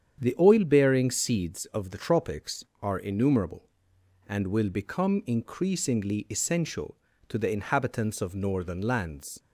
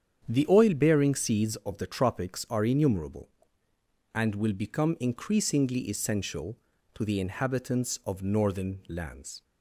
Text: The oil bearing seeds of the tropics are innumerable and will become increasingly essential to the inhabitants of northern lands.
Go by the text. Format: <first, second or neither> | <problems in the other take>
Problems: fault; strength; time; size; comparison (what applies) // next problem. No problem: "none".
neither | starts louder than the rest; strong; the same in both